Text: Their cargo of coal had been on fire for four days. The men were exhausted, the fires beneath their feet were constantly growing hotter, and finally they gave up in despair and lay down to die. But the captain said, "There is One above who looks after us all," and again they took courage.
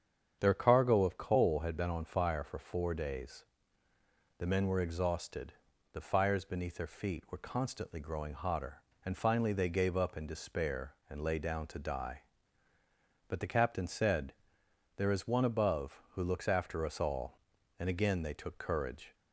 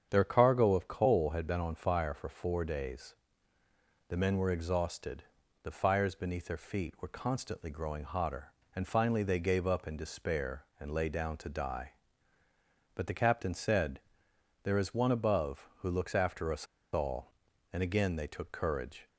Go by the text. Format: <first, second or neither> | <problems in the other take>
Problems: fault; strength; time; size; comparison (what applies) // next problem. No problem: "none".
first | starts louder than the rest; strong; until 1.1 s; 8 dB; strong in the first // pauses between "us" and "all"; slight; at 16.6 s; 0.29 s long